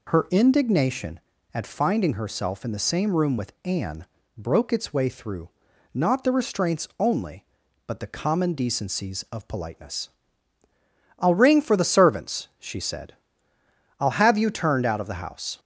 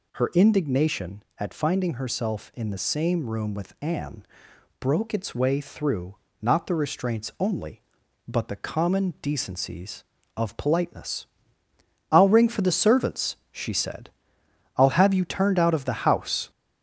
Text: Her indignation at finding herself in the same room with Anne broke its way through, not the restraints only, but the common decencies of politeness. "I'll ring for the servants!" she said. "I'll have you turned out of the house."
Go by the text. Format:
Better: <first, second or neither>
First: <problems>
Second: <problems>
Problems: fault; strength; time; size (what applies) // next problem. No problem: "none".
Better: first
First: pauses between "Anne" and "broke"; slight; at 4.0 s; 0.32 s long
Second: gets louder; noticeable; throughout; 4.5 dB // pauses between "Anne" and "broke"; noticeable; at 4.2 s; 0.54 s long